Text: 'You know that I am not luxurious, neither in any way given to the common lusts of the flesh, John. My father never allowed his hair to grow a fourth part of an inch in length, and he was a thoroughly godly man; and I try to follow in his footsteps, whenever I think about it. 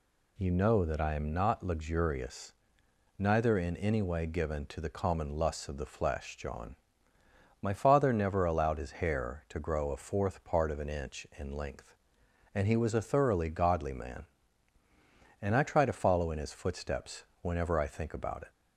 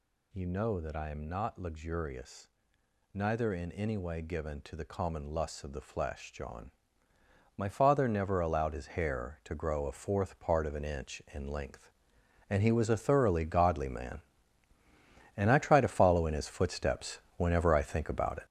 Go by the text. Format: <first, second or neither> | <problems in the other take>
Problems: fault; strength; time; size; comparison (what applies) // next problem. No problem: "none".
first | gets louder; strong; throughout; 7.5 dB